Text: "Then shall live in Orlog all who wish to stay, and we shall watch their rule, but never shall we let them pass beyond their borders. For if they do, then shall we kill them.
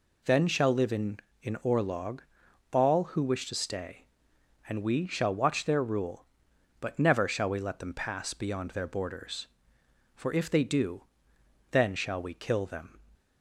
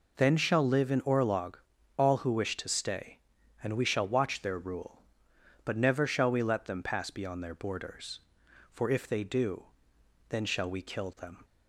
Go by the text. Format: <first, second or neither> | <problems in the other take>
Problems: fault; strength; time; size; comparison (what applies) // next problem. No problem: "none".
second | says "in" twice; at 1.4 s // pauses between "Orlog" and "all"; noticeable; at 2.2 s; 0.50 s long; also in the second